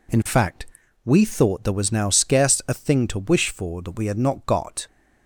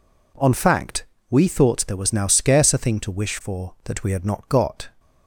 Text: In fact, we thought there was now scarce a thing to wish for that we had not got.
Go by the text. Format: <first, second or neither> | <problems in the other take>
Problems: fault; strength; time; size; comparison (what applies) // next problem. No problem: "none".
first | says "On" for "In"; at 0.3 s